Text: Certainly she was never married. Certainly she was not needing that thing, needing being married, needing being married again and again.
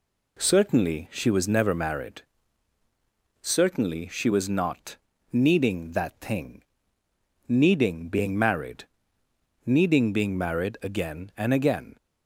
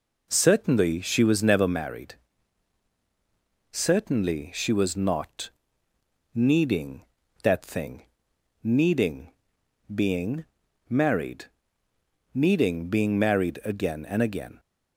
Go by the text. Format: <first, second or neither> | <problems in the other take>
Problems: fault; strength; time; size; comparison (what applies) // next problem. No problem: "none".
first | starts louder than the rest; noticeable; until 1.8 s; 4 dB // pauses between "not" and "needing"; noticeable; at 5.4 s; 0.86 s long; slight in the first // pauses between "needing" and "being"; noticeable; at 9.3 s; 0.64 s long // pauses between "being" and "married"; at 10.4 s; 0.45 s long